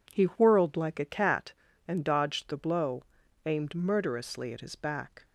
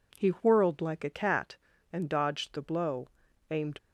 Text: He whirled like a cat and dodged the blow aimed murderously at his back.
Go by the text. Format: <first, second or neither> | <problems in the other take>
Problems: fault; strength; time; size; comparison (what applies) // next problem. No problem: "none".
first | pauses between "blow" and "aimed"; at 3.0 s; 0.40 s long; also in the first // stops before "murderously at his back"; at 3.7 s